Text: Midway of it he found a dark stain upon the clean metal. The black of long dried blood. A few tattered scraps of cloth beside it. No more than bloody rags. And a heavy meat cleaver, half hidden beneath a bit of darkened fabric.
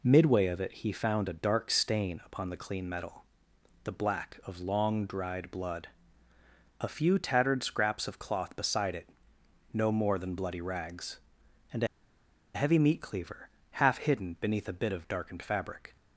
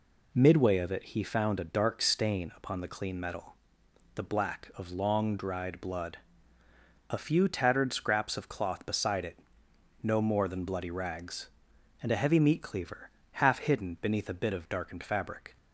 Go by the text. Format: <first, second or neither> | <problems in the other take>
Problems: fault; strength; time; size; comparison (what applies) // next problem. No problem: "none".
second | pauses between "a" and "heavy"; noticeable; at 11.8 s; 0.68 s long